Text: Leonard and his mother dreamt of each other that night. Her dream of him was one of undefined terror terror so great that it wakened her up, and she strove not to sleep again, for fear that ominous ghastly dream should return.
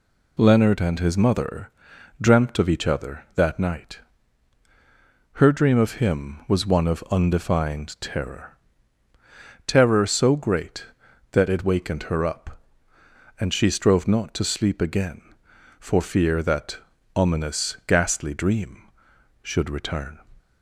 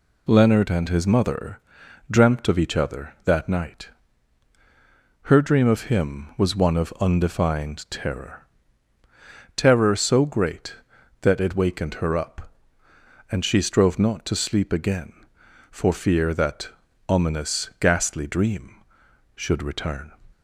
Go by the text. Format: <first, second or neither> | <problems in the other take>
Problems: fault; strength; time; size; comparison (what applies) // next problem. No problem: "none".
neither | pauses between "mother" and "dreamt"; noticeable; the same in both // pauses between "terror" and "terror"; the same in both // pauses between "that" and "ominous"; the same in both